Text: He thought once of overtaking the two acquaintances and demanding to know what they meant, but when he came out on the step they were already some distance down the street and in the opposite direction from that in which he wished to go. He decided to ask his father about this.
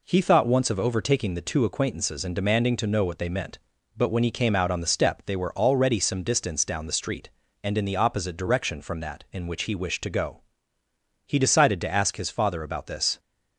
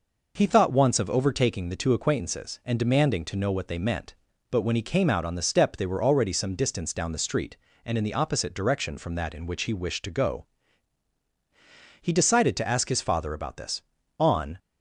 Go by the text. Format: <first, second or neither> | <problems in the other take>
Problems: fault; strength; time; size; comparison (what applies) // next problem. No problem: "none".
first | goes on to say "On"; slight; from 14.2 s on; 0.38 s long